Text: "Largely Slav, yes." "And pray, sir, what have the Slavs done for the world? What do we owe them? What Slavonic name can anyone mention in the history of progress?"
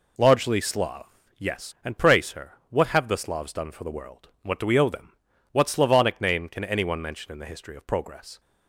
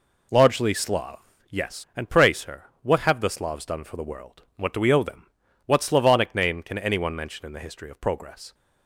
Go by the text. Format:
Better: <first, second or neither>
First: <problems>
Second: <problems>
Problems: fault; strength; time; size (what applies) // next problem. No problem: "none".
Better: neither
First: none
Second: none